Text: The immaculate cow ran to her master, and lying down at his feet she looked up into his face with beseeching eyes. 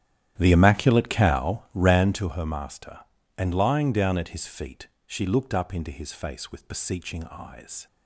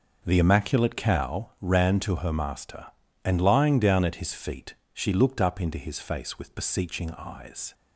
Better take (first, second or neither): second